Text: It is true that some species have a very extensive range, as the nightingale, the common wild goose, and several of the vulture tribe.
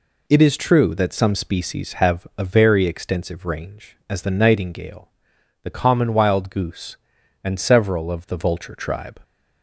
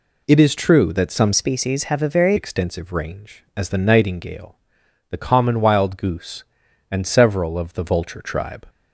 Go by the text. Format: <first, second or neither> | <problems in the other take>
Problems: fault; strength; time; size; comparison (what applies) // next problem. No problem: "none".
first | changes voice from "species" to "very"; from 1.3 to 2.3 s; 1.0 s long